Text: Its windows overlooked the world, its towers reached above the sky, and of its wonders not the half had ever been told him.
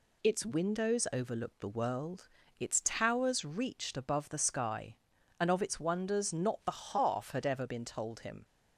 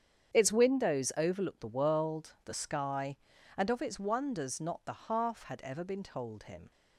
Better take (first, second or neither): first